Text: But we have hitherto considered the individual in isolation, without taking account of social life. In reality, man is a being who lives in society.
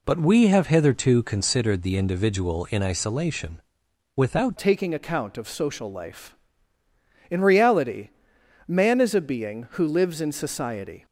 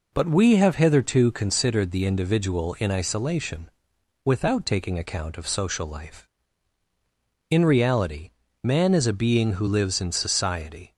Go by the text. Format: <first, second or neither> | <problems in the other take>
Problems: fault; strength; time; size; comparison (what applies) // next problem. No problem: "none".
second | changes voice at "taking"; from 4.5 s on; 6.5 s long